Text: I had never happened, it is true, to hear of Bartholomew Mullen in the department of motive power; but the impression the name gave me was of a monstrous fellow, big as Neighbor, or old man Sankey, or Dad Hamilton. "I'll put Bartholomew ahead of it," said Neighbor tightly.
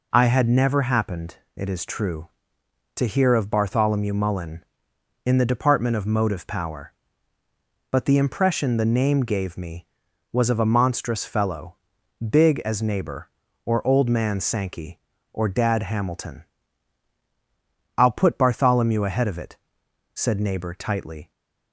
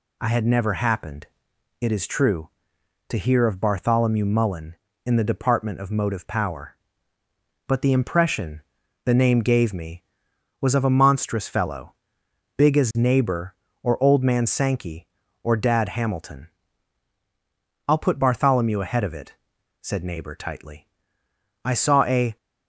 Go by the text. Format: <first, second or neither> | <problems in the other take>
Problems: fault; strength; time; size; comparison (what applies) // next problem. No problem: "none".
first | pauses between "impression" and "the"; at 8.6 s; 0.44 s long // goes on to say "I saw a"; noticeable; from 21.6 s on; 0.72 s long